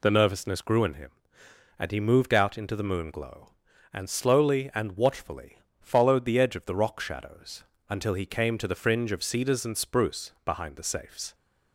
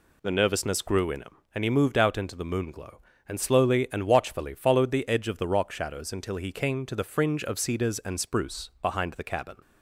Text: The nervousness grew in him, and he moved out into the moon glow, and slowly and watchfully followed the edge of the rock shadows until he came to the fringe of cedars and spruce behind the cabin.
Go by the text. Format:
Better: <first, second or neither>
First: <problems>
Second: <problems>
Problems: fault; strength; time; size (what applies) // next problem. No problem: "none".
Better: second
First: pauses between "watchfully" and "followed"; slight; at 5.5 s; 0.22 s long // pauses between "shadows" and "until"; slight; at 7.6 s; 0.26 s long // says "safes" for "cabin"; at 10.8 s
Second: none